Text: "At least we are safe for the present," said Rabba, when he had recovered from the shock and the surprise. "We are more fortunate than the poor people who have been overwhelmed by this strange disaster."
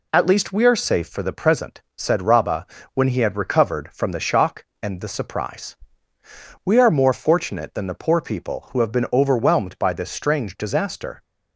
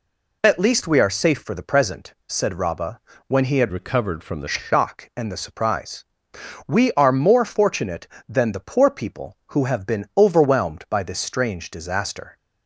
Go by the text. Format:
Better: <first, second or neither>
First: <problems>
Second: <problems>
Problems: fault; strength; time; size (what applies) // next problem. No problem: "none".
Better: first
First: none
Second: changes voice from "recovered" to "the"; from 3.6 to 4.4 s; 0.8 s long